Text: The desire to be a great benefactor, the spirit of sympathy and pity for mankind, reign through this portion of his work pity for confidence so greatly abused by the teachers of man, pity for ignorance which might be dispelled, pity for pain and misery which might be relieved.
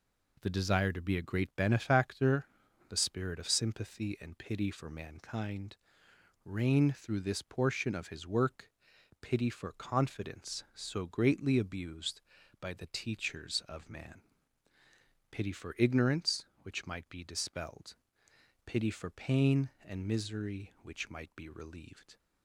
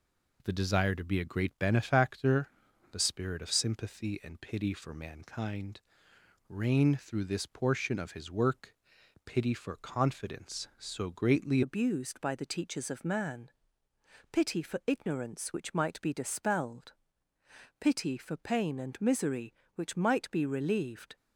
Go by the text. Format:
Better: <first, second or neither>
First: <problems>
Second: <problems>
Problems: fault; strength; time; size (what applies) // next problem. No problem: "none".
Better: first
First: pauses between "work" and "pity"; noticeable; at 8.6 s; 0.54 s long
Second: pauses between "work" and "pity"; noticeable; at 8.7 s; 0.54 s long // changes voice at "abused"; from 11.6 s on; 9.5 s long